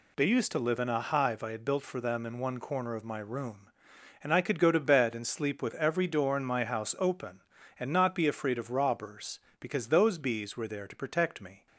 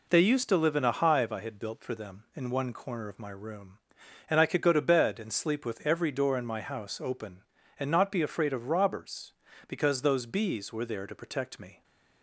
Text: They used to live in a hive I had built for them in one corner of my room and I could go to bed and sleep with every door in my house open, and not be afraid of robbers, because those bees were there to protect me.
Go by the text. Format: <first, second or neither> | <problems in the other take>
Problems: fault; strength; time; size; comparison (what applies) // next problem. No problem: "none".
neither | none